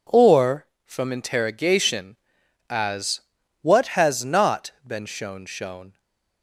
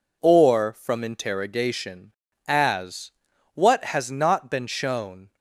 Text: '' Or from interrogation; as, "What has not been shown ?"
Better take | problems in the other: second | says "shown" twice; at 5.4 s // stays silent after the last word; slight; from 5.9 s on; 0.5 s long

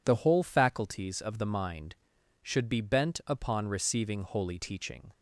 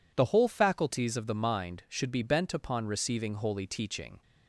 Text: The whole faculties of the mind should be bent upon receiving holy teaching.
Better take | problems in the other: neither | none

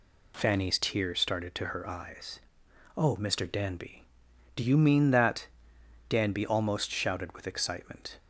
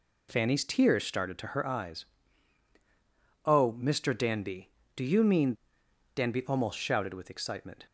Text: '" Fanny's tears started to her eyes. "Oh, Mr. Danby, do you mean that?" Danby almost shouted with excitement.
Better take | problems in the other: first | skips "that"; at 5.8 s

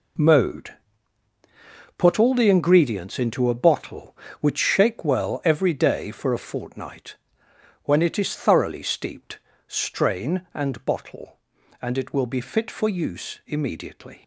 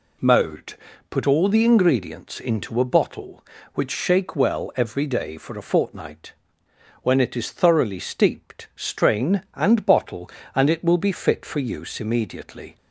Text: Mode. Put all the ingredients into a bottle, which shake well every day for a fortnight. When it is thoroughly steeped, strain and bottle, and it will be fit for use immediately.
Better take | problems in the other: second | gets quieter; strong; throughout; 10 dB

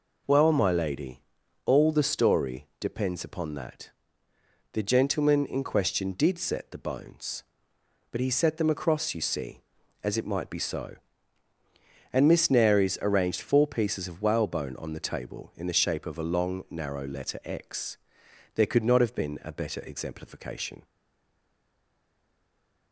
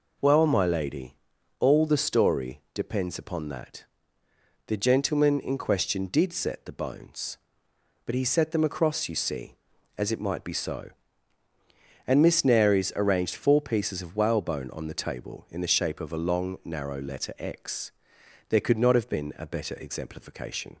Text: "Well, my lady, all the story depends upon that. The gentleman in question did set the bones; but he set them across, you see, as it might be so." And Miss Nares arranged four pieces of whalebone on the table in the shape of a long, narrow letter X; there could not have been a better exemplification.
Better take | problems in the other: second | stays silent after the last word; noticeable; from 20.8 s on; 2.1 s long

